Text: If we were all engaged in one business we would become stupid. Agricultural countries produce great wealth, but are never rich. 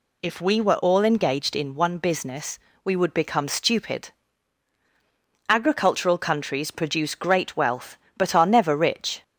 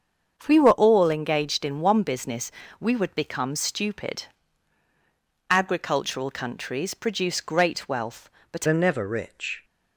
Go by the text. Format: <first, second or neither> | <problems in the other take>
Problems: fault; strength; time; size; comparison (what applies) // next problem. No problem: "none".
first | starts louder than the rest; until 1.3 s; 7 dB // pauses between "business" and "we"; slight; at 2.5 s; 0.28 s long; slight in the first // changes voice at "are"; from 8.6 s on; 1.0 s long